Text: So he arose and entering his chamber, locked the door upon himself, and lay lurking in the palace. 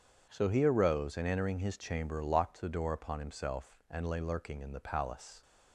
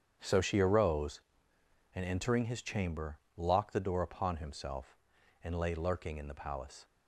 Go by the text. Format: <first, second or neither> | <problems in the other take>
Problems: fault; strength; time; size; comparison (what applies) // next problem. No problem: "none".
first | starts louder than the rest; strong; until 1.9 s; 8 dB; strong in the first // says "she" for "he"; at 0.4 s